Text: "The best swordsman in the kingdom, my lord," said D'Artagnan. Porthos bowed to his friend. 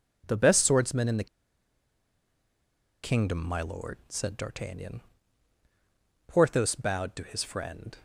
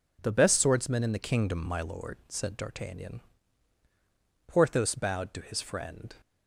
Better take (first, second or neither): second